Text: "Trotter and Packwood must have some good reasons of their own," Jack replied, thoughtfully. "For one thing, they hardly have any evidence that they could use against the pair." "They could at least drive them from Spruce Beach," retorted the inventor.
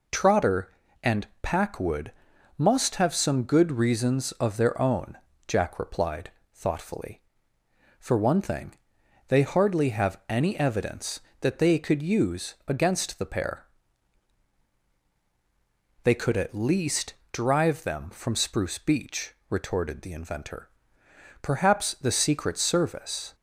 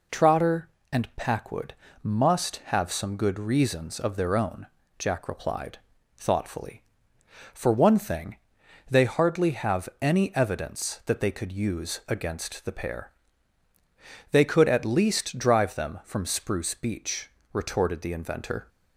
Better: second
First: pauses between "and" and "Packwood"; slight; at 1.2 s; 0.16 s long // pauses between "Packwood" and "must"; at 2.1 s; 0.44 s long // pauses between "least" and "drive"; slight; at 17.1 s; 0.18 s long // goes on to say "Perhaps the Secret Service"; strong; from 21.4 s on; 1.9 s long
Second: pauses between "Packwood" and "must"; slight; at 1.7 s; 0.28 s long

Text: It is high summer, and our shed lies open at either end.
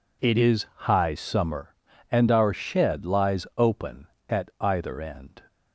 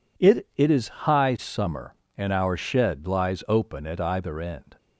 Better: first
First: none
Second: says "It" twice; at 0.5 s

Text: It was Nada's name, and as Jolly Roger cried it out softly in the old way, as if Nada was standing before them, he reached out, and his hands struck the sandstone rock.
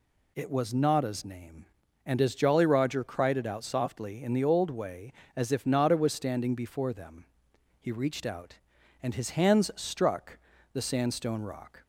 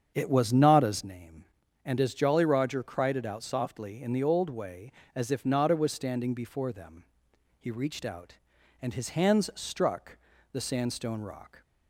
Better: first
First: pauses between "struck" and "the"; slight; at 10.3 s; 0.34 s long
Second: starts louder than the rest; strong; until 1.1 s; 7.5 dB // pauses between "struck" and "the"; slight; at 10.1 s; 0.34 s long

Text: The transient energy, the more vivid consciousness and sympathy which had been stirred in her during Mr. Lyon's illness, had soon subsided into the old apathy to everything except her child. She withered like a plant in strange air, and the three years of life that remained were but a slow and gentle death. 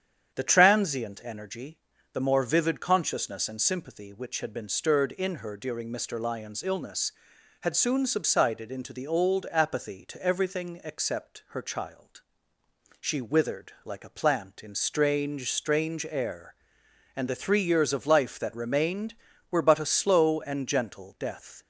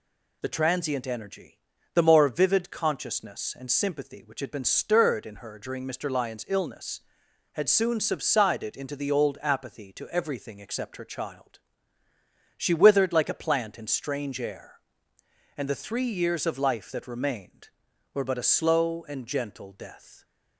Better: second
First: starts louder than the rest; strong; until 1.3 s; 8.5 dB // says "strange" twice; at 15.5 s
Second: none

